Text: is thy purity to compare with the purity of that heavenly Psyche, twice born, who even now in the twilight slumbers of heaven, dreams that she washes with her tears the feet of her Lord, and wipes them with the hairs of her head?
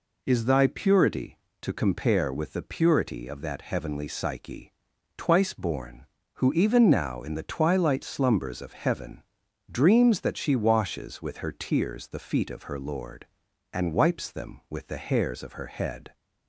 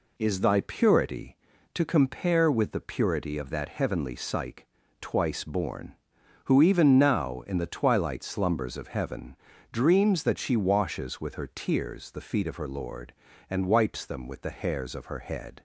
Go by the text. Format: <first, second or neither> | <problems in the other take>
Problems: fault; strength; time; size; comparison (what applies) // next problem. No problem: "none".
neither | none